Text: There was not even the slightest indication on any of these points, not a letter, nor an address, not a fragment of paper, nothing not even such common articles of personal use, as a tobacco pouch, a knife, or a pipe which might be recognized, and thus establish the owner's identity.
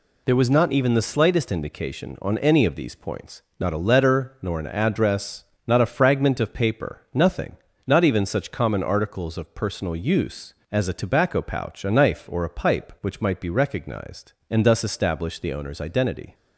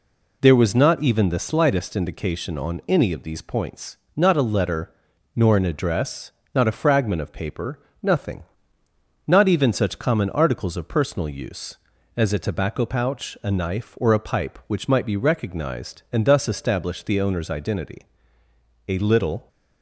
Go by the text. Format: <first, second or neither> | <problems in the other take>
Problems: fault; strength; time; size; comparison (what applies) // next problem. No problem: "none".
first | pauses between "nothing" and "not"; noticeable; at 8.4 s; 0.86 s long; slight in the first // goes on to say "A little"; from 18.8 s on; 0.60 s long